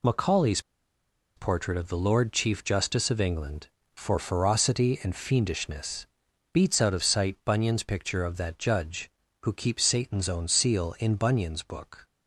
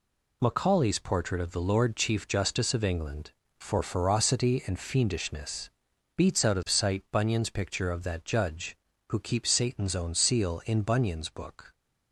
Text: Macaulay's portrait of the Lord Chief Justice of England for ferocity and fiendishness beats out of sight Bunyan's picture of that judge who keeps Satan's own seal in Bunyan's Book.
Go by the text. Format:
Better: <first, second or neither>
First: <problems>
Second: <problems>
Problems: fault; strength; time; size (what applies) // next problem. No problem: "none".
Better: second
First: pauses between "Macaulay's" and "portrait"; noticeable; at 0.6 s; 0.76 s long // pauses between "fiendishness" and "beats"; noticeable; at 6.0 s; 0.48 s long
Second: pauses between "fiendishness" and "beats"; noticeable; at 5.6 s; 0.48 s long